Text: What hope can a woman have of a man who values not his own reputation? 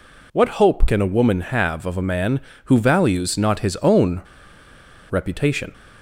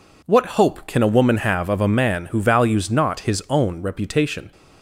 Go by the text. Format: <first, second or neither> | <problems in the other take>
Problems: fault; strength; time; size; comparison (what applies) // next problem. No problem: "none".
second | pauses between "own" and "reputation"; noticeable; at 4.2 s; 0.89 s long